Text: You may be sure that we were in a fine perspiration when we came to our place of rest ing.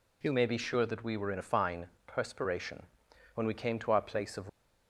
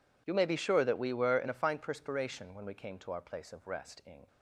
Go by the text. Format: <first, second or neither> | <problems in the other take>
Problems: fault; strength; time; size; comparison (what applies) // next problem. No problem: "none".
second | pauses between "fine" and "perspiration"; slight; at 1.8 s; 0.20 s long // pauses between "perspiration" and "when"; noticeable; at 2.8 s; 0.54 s long // stops before "rest ing"; at 4.4 s